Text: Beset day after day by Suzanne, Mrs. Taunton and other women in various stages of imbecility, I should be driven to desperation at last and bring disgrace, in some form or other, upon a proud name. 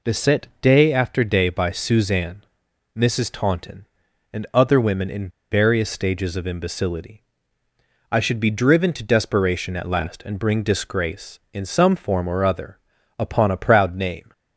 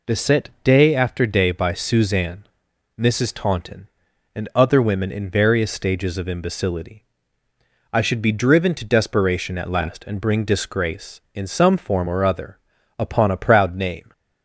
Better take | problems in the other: second | pauses between "in" and "various"; slight; at 5.2 s; 0.22 s long

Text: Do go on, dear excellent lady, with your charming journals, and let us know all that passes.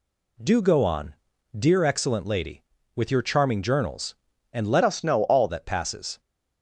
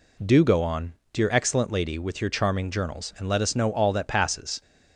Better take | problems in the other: second | changes voice from "us" to "all"; from 4.8 to 5.4 s; 0.6 s long

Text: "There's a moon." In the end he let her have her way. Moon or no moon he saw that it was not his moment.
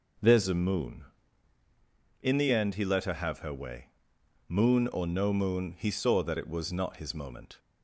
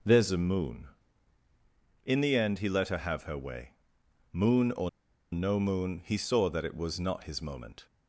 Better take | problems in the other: first | pauses between "or" and "no"; at 4.8 s; 0.42 s long

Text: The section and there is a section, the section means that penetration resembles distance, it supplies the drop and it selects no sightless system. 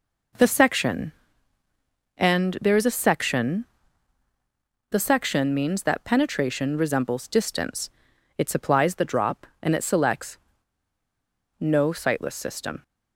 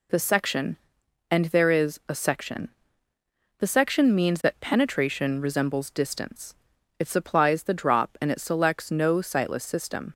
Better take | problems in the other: second | pauses between "selects" and "no"; at 10.3 s; 1.2 s long

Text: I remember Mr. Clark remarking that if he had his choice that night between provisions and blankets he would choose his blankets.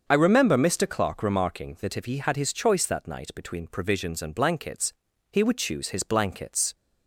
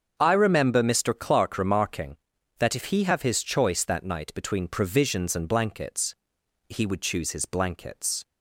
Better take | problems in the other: first | starts louder than the rest; until 1.1 s; 7 dB; also in the first // says "have" for "had"; at 3.0 s // pauses between "blankets" and "he"; noticeable; at 6.1 s; 0.54 s long; also in the first

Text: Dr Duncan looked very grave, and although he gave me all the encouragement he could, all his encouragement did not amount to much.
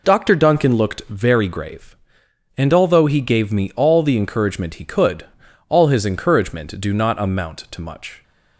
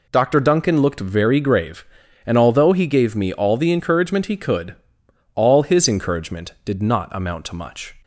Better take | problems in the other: second | says "do" for "did"; at 6.7 s

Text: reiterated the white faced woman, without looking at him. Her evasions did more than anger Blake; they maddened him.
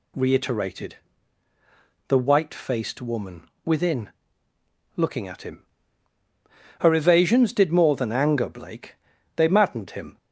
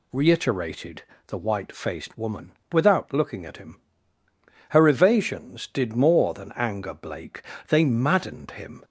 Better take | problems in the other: second | pauses between "reiterated" and "the"; at 0.9 s; 1.1 s long; slight in the second // says "within" for "without"; at 3.6 s

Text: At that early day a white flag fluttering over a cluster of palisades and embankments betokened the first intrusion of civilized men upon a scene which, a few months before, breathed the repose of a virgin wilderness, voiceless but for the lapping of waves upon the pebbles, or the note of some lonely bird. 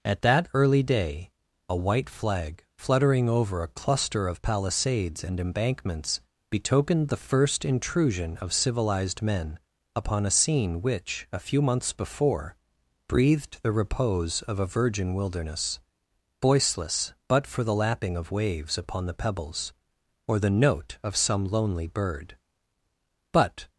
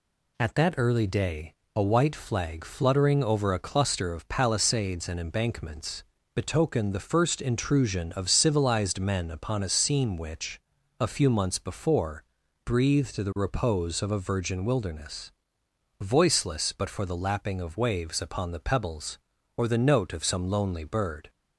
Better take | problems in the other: second | pauses between "day" and "a"; at 1.3 s; 0.38 s long; slight in the second // pauses between "embankments" and "betokened"; slight; at 6.2 s; 0.28 s long; slight in the second // pauses between "men" and "upon"; slight; at 9.5 s; 0.36 s long // goes on to say "But"; slight; from 23.3 s on; 0.36 s long

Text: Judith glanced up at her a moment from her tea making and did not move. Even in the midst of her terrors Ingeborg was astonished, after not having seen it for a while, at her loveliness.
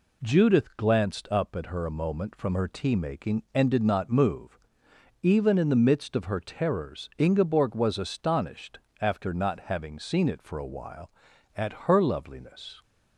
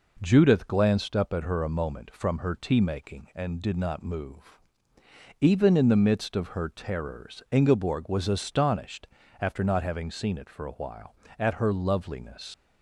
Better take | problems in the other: first | leaves "loveliness" unfinished; at 12.5 s; 95 ms

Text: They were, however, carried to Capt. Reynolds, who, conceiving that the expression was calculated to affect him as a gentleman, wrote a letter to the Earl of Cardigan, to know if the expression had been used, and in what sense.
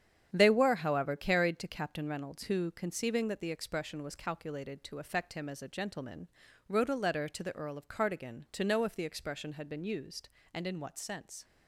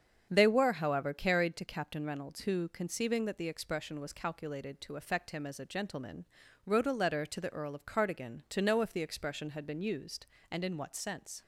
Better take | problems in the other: second | gets quieter; strong; throughout; 8 dB // starts louder than the rest; strong; until 1.3 s; 9 dB; strong in the second

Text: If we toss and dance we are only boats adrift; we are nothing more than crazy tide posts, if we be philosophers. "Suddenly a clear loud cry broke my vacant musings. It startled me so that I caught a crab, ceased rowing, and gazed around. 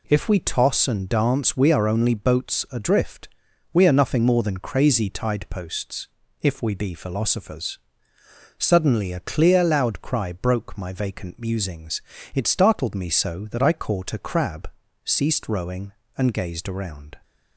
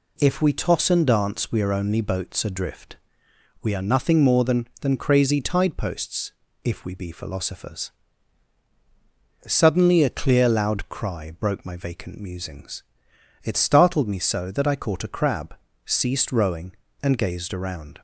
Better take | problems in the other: first | says "than" twice; at 4.8 s

